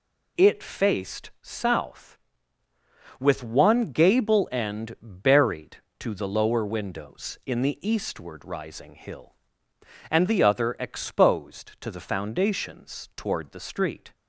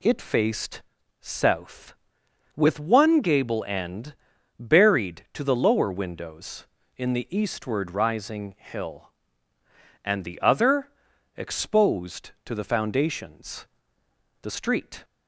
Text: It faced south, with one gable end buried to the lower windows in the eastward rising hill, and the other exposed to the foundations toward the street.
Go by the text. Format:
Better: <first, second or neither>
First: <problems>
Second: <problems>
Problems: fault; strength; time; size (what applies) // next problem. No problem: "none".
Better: first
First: none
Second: pauses between "faced" and "south"; at 0.8 s; 0.38 s long // pauses between "end" and "buried"; at 4.1 s; 0.42 s long // pauses between "other" and "exposed"; noticeable; at 10.8 s; 0.48 s long // skips "toward"; at 14.0 s